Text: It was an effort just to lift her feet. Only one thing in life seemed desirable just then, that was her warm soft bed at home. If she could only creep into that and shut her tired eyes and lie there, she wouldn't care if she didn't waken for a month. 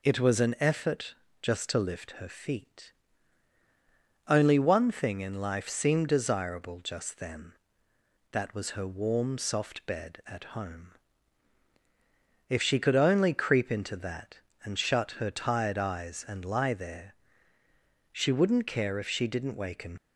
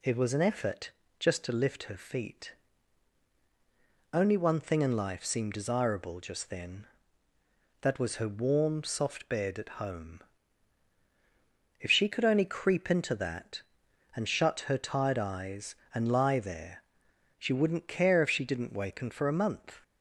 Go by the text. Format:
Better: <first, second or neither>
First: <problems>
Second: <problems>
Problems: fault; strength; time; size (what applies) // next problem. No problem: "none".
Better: second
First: pauses between "effort" and "just"; slight; at 1.1 s; 0.26 s long // stops before "for a month"; at 19.9 s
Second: pauses between "effort" and "just"; slight; at 0.9 s; 0.28 s long